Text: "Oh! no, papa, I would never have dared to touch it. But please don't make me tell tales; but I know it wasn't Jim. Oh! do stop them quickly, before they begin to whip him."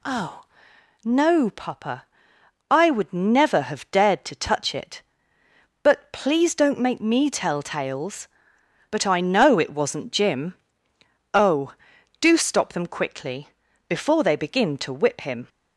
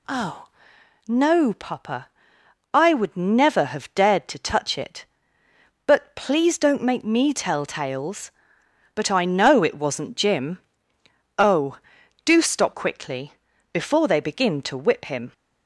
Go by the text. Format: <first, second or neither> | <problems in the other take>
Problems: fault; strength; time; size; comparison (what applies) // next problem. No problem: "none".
first | skips "them"; at 12.7 s